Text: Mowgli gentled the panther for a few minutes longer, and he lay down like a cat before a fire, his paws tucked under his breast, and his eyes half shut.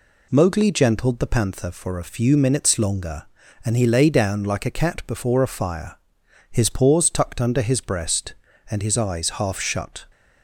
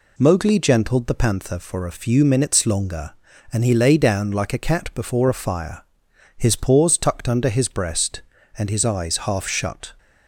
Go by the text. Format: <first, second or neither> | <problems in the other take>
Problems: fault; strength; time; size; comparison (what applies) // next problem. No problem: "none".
neither | none